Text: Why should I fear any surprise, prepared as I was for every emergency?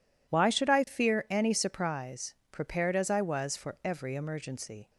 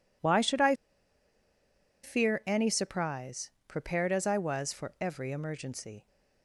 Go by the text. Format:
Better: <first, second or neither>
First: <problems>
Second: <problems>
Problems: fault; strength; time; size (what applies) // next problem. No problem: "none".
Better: first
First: none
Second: pauses between "I" and "fear"; strong; at 0.7 s; 1.3 s long